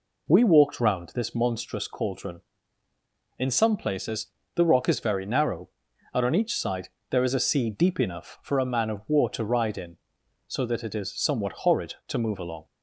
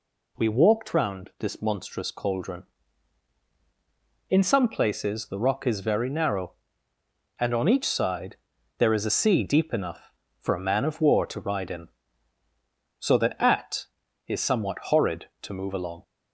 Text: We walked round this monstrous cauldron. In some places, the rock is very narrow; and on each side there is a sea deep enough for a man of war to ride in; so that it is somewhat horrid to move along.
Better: first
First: pauses between "side" and "there"; slight; at 6.8 s; 0.20 s long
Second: pauses between "side" and "there"; at 8.3 s; 0.42 s long // says "at" for "it"; at 13.3 s

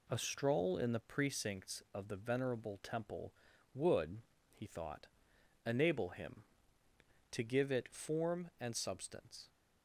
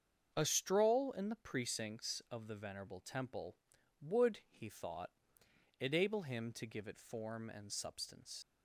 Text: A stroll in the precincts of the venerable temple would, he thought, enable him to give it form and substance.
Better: first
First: none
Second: starts louder than the rest; until 1.3 s; 7 dB // leaves "substance" unfinished; at 8.4 s; 80 ms

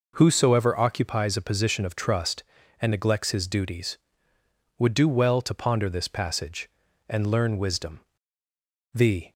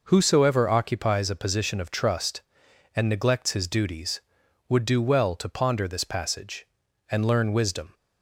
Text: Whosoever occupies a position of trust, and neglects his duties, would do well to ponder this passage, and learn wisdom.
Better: second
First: goes on to say "The"; slight; from 8.9 s on; 0.38 s long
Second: none

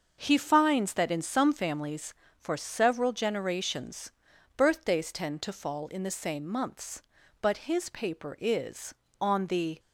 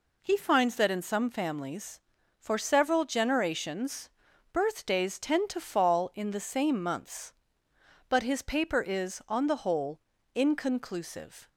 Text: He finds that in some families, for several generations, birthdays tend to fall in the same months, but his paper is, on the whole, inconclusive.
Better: second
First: starts louder than the rest; until 1.2 s; 6.5 dB // stops before "whole inconclusive"; at 9.7 s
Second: none

